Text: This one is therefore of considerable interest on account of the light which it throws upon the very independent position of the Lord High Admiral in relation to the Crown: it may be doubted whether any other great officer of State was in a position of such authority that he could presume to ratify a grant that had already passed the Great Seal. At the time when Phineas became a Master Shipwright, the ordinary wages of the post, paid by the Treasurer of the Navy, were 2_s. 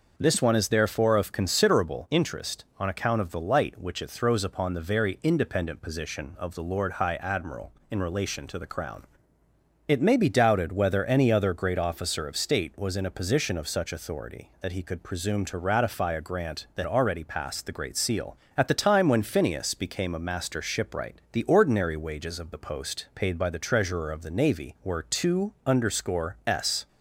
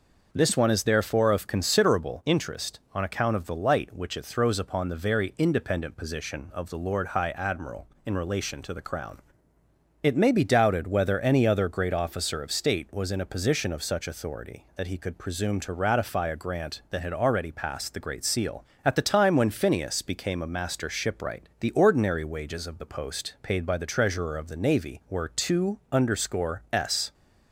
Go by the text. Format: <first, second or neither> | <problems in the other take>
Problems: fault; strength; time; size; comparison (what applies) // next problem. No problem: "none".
second | skips "had"; at 16.8 s